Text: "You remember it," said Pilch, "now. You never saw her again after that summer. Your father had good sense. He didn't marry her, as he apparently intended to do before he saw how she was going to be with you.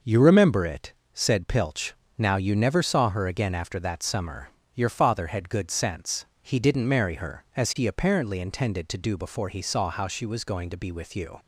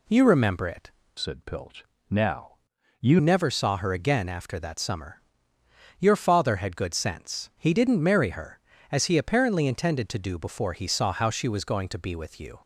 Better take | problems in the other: first | changes voice from "said" to "You"; from 1.1 to 3.1 s; 2.0 s long

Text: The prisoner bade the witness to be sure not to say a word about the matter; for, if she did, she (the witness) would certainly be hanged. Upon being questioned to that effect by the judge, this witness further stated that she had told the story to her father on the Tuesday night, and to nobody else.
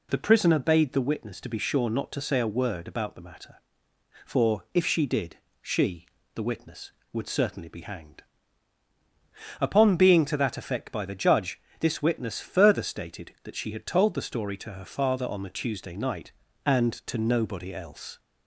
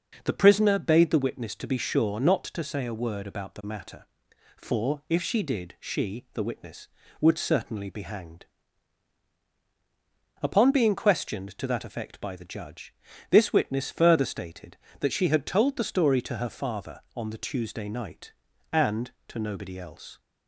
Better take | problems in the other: second | skips "questioned"; at 10.2 s

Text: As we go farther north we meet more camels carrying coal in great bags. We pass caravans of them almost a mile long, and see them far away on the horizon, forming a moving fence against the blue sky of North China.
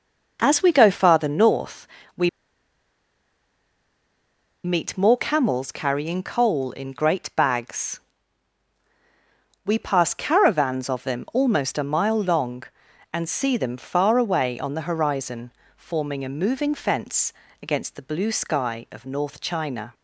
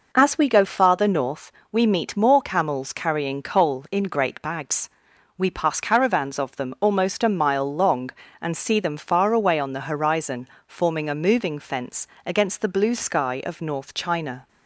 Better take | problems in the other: second | pauses between "north" and "we"; slight; at 1.8 s; 0.30 s long; slight in the second // pauses between "we" and "meet"; strong; at 2.2 s; 2.3 s long // pauses between "fence" and "against"; slight; at 17.3 s; 0.30 s long; slight in the second

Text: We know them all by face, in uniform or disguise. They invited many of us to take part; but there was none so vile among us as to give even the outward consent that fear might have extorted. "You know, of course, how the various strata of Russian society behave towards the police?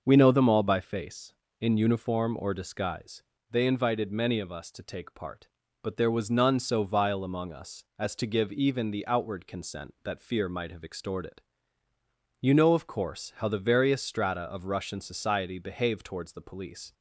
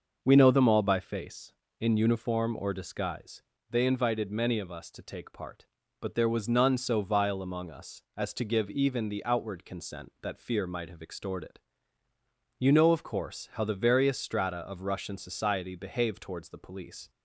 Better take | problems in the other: neither | starts louder than the rest; noticeable; the same in both

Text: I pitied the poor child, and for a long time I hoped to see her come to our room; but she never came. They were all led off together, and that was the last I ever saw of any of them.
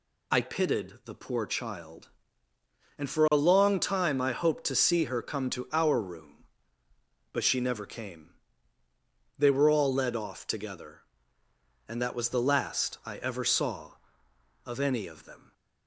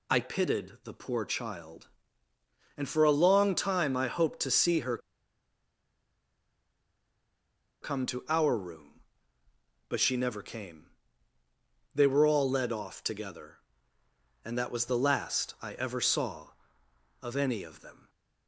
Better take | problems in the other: first | pauses between "her" and "come"; strong; at 4.9 s; 2.8 s long

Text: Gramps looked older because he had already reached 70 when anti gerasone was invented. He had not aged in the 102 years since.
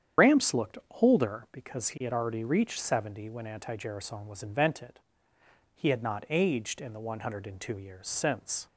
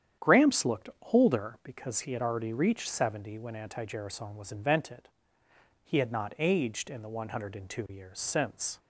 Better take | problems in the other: second | loses the start of "Gramps"; at 0.1 s; 95 ms // starts louder than the rest; strong; until 1.4 s; 8.5 dB; strong in the second // pauses between "looked" and "older"; slight; at 0.7 s; 0.24 s long; slight in the second

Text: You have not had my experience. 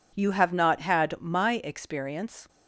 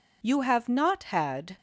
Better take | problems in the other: first | stops before "my experience"; at 1.5 s

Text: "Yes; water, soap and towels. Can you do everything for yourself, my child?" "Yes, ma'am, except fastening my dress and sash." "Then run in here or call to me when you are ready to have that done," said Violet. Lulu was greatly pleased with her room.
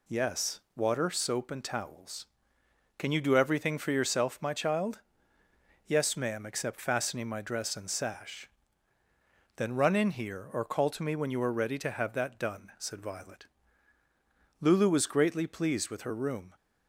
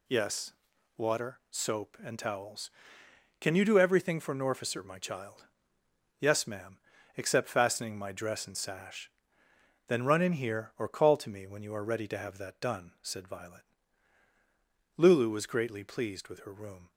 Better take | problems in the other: first | says "norficer" for "yourself"; at 4.3 s

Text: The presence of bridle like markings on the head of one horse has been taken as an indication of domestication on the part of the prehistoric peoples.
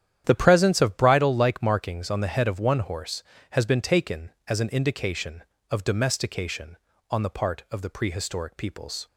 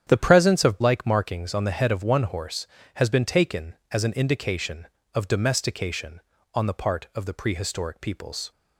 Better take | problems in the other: first | starts louder than the rest; strong; until 1.0 s; 9 dB; strong in the first // skips "bridle"; at 0.7 s

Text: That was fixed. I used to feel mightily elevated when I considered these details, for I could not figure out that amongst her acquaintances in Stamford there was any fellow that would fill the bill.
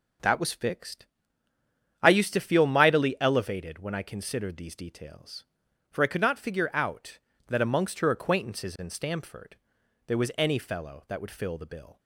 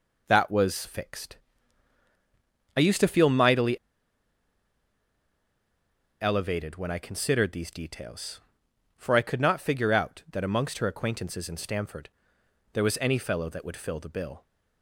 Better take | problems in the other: first | pauses between "mightily" and "elevated"; strong; at 3.7 s; 2.4 s long // pauses between "Stamford" and "there"; noticeable; at 12.0 s; 0.64 s long; noticeable in the first

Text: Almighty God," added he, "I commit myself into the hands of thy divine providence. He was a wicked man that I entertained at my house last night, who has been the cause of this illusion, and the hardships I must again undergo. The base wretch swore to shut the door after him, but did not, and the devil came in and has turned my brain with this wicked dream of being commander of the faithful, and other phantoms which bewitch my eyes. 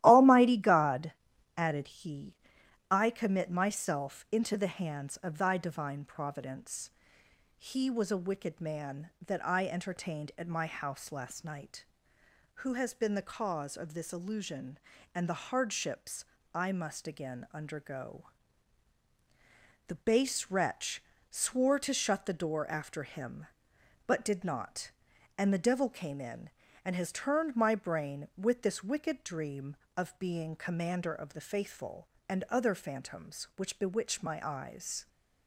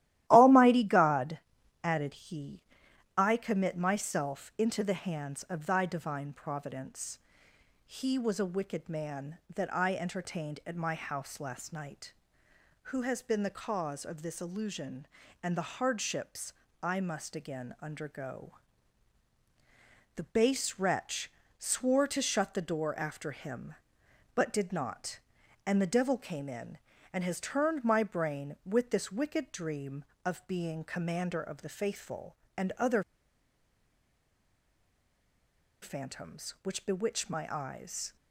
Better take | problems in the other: first | starts louder than the rest; strong; until 1.2 s; 14 dB; strong in the first // pauses between "hardships" and "I"; slight; at 16.5 s; 0.32 s long; slight in the first // pauses between "wretch" and "swore"; slight; at 21.3 s; 0.26 s long; slight in the first // pauses between "other" and "phantoms"; strong; at 33.0 s; 2.8 s long

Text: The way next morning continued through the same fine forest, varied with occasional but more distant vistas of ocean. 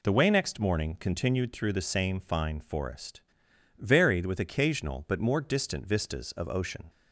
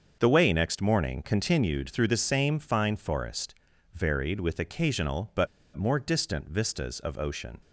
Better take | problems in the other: first | starts louder than the rest; until 1.2 s; 6.5 dB // pauses between "but" and "more"; slight; at 5.4 s; 0.29 s long

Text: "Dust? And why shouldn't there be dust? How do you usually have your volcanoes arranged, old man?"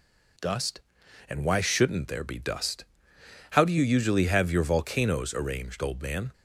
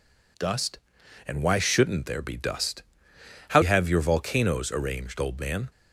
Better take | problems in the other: first | skips "do you usually"; at 3.6 s

